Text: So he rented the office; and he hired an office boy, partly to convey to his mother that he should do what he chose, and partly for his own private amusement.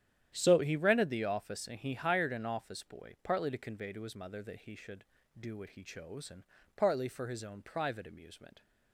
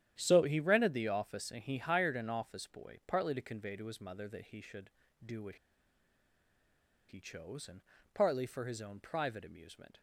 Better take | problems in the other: first | starts louder than the rest; strong; until 1.1 s; 10.5 dB; strong in the first // pauses between "what" and "he"; strong; at 5.5 s; 1.5 s long // pauses between "and" and "partly"; slight; at 7.8 s; 0.32 s long; slight in the first

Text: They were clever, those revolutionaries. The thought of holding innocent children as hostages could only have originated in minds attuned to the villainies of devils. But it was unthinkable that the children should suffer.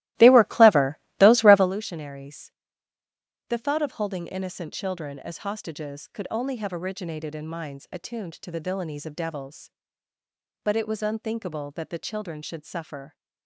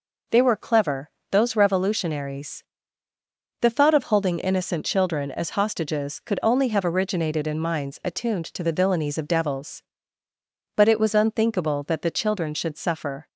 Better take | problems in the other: second | starts louder than the rest; strong; until 1.7 s; 16.5 dB

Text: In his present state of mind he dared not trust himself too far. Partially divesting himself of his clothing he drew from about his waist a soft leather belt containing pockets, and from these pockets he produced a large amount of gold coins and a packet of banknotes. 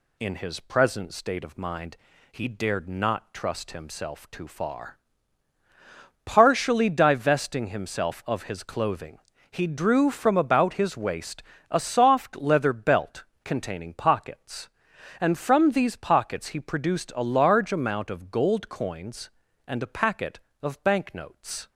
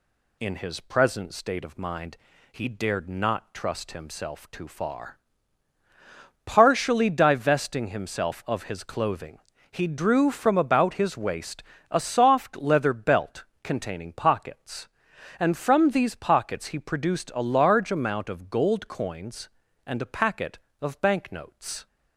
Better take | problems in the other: neither | pauses between "mind" and "he"; slight; the same in both // pauses between "clothing" and "he"; slight; the same in both // pauses between "waist" and "a"; slight; the same in both // pauses between "belt" and "containing"; slight; the same in both

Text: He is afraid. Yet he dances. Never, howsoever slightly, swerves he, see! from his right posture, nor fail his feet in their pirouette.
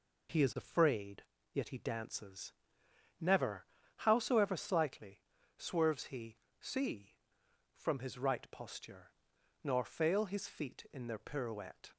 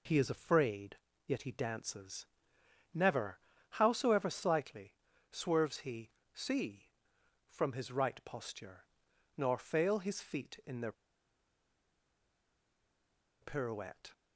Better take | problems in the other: first | pauses between "their" and "pirouette"; strong; at 10.9 s; 2.4 s long

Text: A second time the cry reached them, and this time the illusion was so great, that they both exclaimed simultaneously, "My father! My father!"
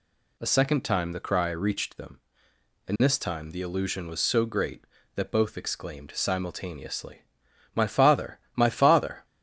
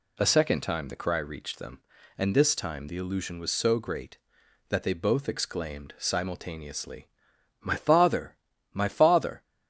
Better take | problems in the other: second | skips "they"; at 5.3 s

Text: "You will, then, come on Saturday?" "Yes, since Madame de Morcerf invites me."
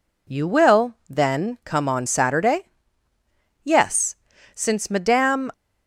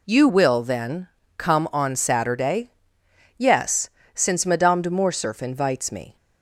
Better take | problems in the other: second | stops before "de Morcerf invites me"; at 5.5 s

